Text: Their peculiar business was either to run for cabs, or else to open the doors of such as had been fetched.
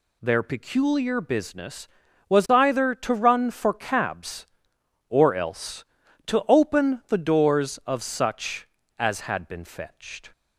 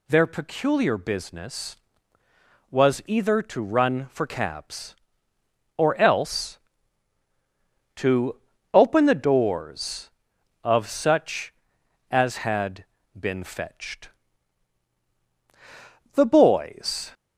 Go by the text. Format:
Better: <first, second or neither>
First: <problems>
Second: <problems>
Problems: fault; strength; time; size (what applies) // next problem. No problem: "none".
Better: first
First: none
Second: pauses between "to" and "open"; slight; at 8.3 s; 0.36 s long // pauses between "had" and "been"; slight; at 12.8 s; 0.36 s long // goes on to say "The boys"; noticeable; from 16.1 s on; 0.98 s long